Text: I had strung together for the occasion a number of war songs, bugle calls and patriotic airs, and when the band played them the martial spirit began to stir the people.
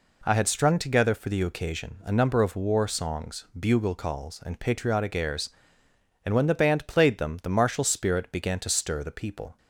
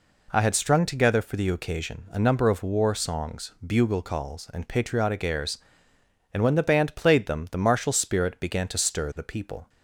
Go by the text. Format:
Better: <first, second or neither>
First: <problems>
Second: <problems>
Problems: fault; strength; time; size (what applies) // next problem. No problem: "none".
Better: neither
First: none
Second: none